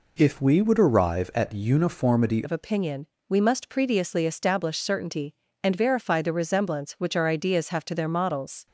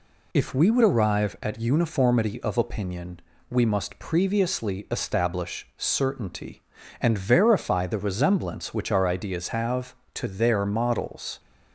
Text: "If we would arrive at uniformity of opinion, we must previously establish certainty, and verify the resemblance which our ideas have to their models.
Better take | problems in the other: second | changes voice at "of"; from 2.4 s on; 6.2 s long

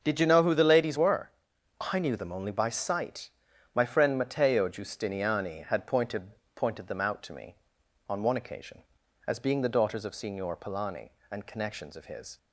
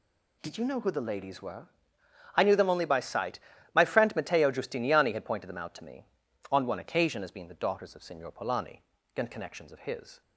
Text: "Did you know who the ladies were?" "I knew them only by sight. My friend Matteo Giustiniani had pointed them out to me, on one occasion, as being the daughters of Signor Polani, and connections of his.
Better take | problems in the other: second | starts louder than the rest; until 1.0 s; 6.5 dB // says "pointed" twice; at 6.5 s

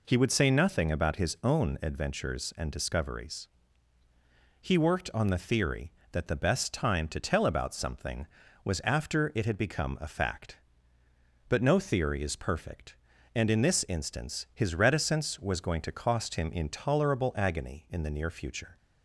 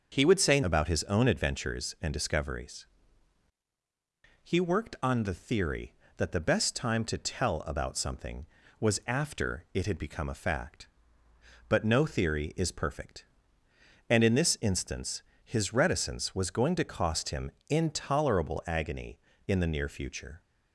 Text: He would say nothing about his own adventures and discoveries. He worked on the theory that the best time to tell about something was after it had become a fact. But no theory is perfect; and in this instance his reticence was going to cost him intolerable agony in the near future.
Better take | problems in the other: first | starts louder than the rest; until 1.1 s; 6 dB // skips "nothing"; at 0.6 s // pauses between "instance" and "his"; slight; at 15.2 s; 0.22 s long // pauses between "him" and "intolerable"; slight; at 17.4 s; 0.20 s long

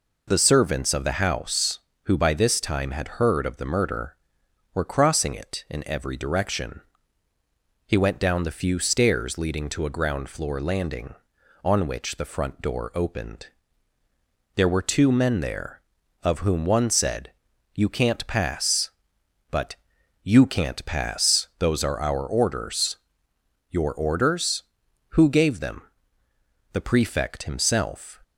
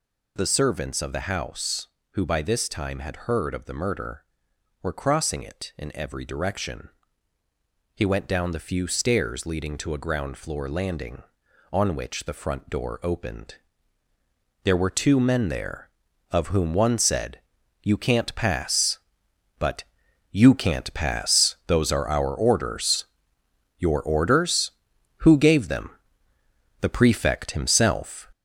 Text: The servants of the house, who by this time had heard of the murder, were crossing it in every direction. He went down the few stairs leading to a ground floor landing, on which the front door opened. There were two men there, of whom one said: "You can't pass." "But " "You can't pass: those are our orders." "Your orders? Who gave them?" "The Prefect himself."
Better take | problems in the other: first | gets louder; noticeable; throughout; 5 dB

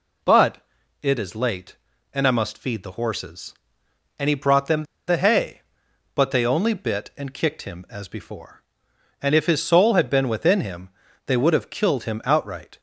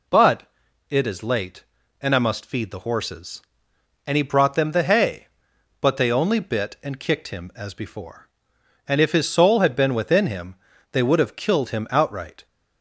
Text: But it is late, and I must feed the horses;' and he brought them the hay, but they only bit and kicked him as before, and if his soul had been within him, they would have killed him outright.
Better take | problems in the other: second | pauses between "But" and "it"; at 0.5 s; 0.44 s long; noticeable in the second // pauses between "them" and "the"; slight; at 4.8 s; 0.24 s long

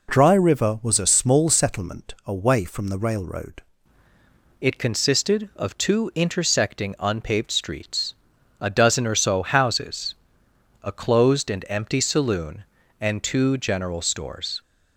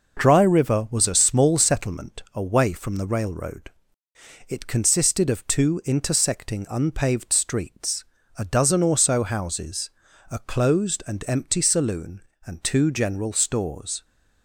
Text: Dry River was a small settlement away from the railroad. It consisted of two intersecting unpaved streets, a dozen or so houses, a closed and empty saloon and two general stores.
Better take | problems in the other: second | changes voice at "It"; from 4.6 s on; 10.0 s long

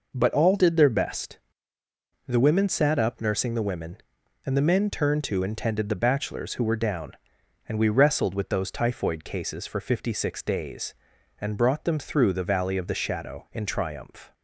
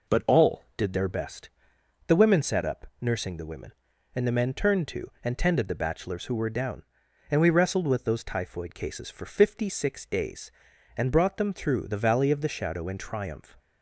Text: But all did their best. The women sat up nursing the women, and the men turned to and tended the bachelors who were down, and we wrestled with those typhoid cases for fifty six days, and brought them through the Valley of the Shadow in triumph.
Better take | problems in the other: neither | none

